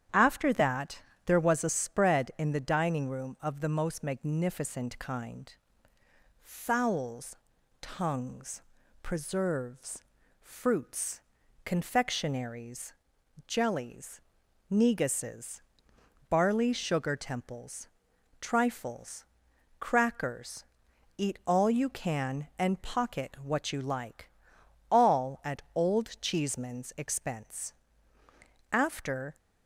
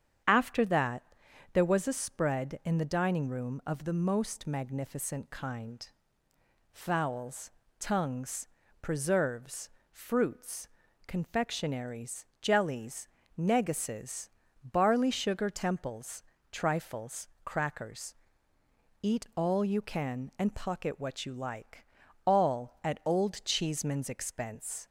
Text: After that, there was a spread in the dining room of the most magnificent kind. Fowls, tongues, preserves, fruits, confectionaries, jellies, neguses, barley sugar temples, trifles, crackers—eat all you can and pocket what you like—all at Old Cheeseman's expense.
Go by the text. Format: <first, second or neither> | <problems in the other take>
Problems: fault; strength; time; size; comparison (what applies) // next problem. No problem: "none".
second | starts louder than the rest; strong; until 1.3 s; 9.5 dB; strong in the second // goes on to say "After"; noticeable; from 28.7 s on; 0.64 s long